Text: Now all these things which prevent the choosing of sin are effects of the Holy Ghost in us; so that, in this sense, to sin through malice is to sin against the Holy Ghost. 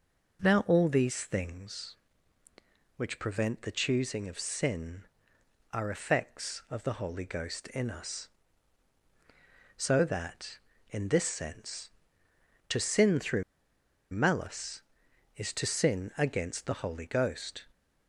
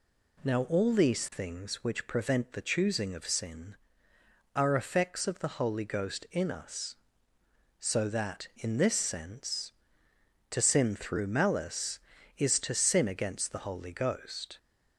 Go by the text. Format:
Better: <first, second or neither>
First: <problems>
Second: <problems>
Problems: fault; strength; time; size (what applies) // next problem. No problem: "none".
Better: second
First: pauses between "through" and "malice"; noticeable; at 13.4 s; 0.68 s long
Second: none